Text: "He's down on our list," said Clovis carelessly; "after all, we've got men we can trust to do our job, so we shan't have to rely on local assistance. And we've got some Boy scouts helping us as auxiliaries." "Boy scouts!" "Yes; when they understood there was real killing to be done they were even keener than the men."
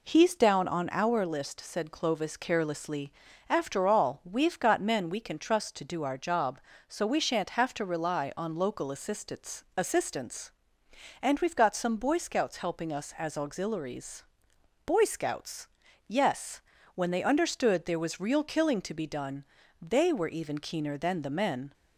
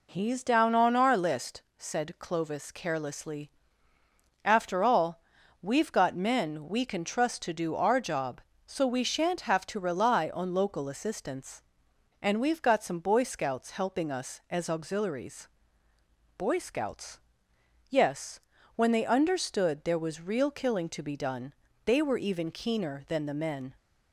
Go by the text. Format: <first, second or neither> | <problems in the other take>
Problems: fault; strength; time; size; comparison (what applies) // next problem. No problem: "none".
second | says "assistance" twice; at 9.7 s // pauses between "done" and "they"; at 19.4 s; 0.38 s long; slight in the second